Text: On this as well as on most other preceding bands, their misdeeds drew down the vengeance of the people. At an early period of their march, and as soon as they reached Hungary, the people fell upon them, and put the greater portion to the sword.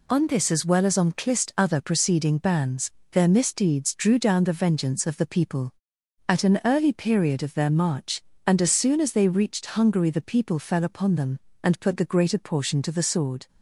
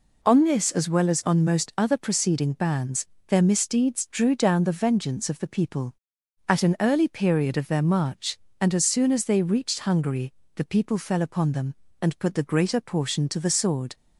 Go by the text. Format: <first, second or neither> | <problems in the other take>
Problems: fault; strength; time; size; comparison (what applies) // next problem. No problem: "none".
second | says "clist" for "most"; at 1.1 s